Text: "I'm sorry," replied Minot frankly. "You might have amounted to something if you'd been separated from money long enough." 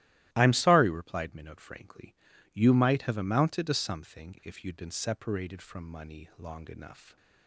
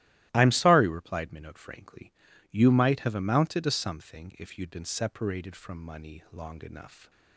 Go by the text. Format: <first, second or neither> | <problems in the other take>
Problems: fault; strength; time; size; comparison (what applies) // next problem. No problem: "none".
neither | starts louder than the rest; strong; the same in both